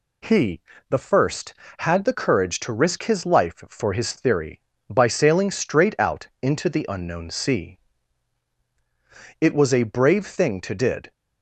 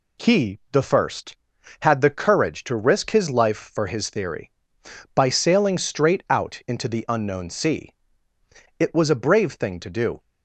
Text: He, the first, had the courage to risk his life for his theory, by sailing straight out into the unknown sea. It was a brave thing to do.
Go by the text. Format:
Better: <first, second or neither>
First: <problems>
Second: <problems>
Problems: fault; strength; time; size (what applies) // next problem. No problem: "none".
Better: second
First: says "did" for "do"; at 10.7 s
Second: none